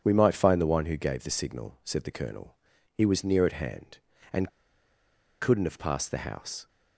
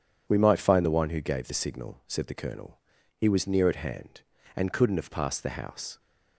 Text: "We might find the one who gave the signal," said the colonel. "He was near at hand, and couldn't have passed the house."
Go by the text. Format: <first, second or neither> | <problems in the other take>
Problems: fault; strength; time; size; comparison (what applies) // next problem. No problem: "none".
second | pauses between "and" and "couldn't"; noticeable; at 4.4 s; 0.91 s long